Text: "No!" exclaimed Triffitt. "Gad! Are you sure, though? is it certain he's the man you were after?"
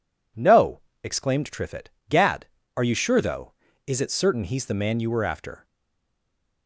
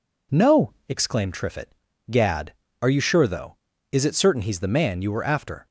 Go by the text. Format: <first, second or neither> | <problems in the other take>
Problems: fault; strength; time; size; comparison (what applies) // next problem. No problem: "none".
second | stays silent after the last word; from 5.6 s on; 1.0 s long